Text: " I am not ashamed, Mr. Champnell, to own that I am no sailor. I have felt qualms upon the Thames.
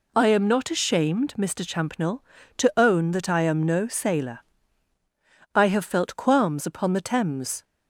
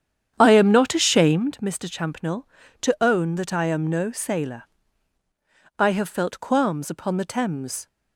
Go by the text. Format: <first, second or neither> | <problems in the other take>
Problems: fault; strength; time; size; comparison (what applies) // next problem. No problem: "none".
first | starts louder than the rest; strong; until 1.5 s; 8.5 dB